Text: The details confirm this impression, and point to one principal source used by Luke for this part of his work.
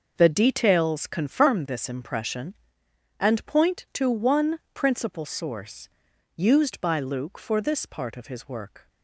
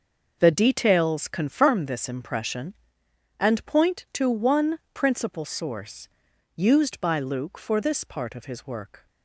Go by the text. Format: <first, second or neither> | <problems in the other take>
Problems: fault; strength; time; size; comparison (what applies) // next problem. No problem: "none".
neither | pauses between "one" and "principal"; slight; the same in both // pauses between "source" and "used"; noticeable; the same in both